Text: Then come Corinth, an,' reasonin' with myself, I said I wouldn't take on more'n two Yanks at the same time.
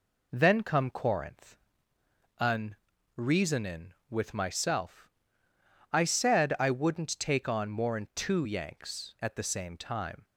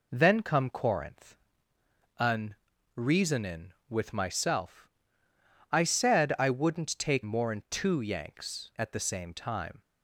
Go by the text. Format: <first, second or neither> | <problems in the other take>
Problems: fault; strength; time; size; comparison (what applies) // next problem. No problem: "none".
first | skips "on"; at 7.2 s